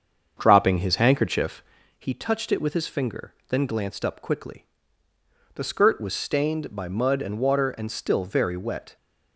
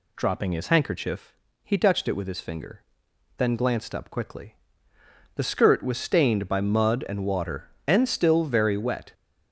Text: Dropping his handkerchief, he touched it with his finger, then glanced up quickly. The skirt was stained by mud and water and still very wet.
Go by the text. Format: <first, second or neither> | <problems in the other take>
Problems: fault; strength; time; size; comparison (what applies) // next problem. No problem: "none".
second | starts louder than the rest; until 1.9 s; 7 dB